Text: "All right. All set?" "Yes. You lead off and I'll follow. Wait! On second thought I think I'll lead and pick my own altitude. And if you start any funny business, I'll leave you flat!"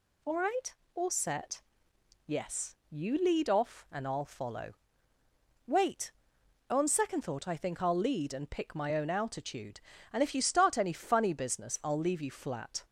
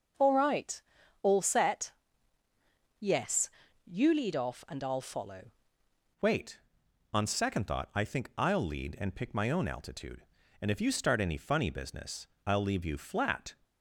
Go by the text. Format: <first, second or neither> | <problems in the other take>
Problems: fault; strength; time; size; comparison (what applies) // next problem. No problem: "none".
first | starts louder than the rest; until 1.5 s; 6 dB // changes voice at "Wait"; from 6.2 s on; 7.3 s long